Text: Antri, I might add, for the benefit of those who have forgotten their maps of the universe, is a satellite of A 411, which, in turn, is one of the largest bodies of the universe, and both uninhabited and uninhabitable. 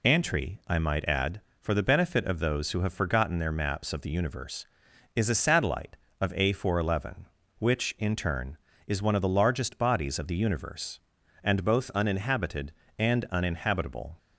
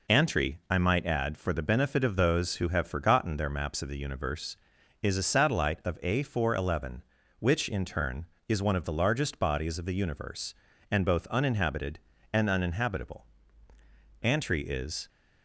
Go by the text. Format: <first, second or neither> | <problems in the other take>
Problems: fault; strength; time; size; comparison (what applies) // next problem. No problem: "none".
first | goes on to say "Antri is"; noticeable; from 14.2 s on; 0.86 s long